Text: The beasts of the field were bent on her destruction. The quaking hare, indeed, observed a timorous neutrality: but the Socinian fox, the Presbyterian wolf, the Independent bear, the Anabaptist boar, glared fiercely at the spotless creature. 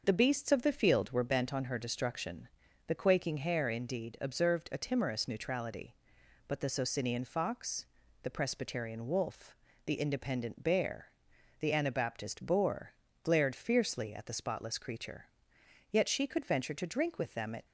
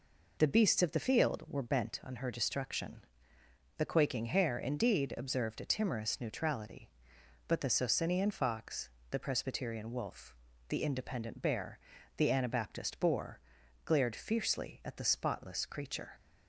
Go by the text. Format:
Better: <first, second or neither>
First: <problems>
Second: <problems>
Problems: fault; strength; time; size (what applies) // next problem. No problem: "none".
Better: second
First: starts louder than the rest; noticeable; until 1.0 s; 6 dB // goes on to say "Yet she could venture to drink with them at"; strong; from 15.9 s on; 1.7 s long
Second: none